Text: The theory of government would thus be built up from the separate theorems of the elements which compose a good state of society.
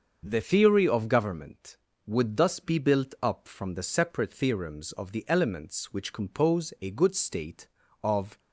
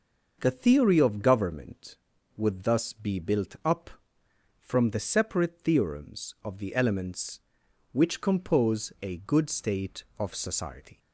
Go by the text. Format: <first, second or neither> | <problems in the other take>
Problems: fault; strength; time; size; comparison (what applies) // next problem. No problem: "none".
second | starts louder than the rest; until 1.2 s; 6.5 dB; noticeable in the second // stops before "society"; at 8.3 s